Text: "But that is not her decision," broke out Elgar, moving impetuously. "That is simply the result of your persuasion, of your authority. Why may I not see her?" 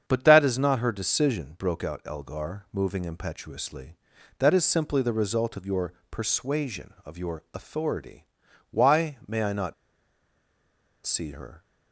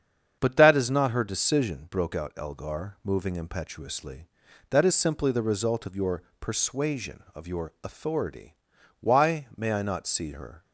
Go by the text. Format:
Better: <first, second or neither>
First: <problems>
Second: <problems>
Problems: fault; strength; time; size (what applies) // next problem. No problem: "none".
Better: second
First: starts louder than the rest; strong; until 1.0 s; 7.5 dB // pauses between "your" and "persuasion"; slight; at 5.9 s; 0.20 s long // pauses between "not" and "see"; strong; at 9.7 s; 1.3 s long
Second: starts louder than the rest; strong; until 1.4 s; 7.5 dB // pauses between "your" and "persuasion"; slight; at 6.2 s; 0.20 s long